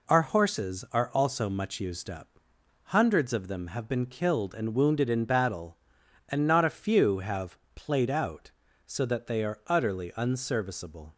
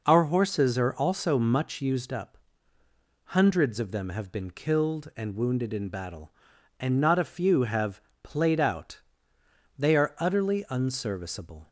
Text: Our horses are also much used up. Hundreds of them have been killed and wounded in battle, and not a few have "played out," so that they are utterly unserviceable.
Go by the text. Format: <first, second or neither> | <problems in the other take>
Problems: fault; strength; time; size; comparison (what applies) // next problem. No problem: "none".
first | pauses between "have" and "played"; slight; at 8.0 s; 0.22 s long; slight in the first // skips "so that"; at 9.3 s